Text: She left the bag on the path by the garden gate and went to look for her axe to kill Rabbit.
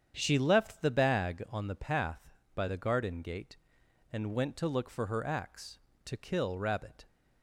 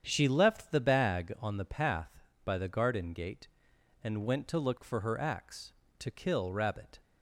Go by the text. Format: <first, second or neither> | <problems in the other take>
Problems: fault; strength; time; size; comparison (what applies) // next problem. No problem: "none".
neither | starts louder than the rest; strong; the same in both